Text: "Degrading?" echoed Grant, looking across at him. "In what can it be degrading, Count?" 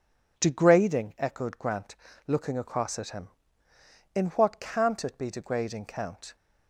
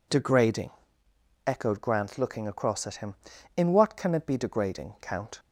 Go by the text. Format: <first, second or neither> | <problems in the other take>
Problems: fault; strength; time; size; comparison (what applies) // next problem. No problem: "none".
second | says "can't" for "can"; at 4.6 s